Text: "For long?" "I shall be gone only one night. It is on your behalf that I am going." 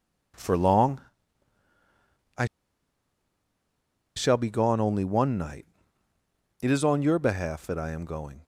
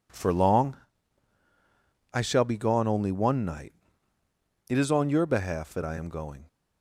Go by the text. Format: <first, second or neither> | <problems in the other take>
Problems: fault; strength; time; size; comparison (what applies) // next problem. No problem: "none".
second | pauses between "I" and "shall"; strong; at 2.4 s; 1.7 s long